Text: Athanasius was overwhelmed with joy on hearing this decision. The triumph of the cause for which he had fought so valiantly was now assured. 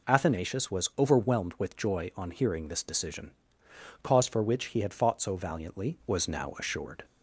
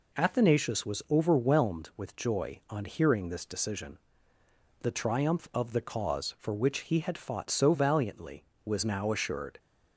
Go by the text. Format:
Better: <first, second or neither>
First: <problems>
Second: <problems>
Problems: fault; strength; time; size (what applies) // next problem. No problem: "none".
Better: second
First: skips "The triumph of the"; at 3.6 s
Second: none